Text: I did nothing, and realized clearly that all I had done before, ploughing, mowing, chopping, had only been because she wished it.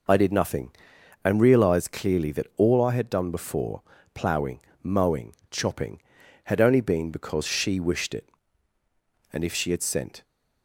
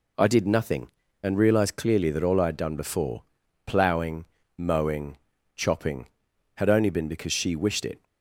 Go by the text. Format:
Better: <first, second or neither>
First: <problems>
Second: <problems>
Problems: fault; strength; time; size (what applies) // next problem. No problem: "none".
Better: second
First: goes on to say "And if she had sent"; noticeable; from 9.3 s on; 0.90 s long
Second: none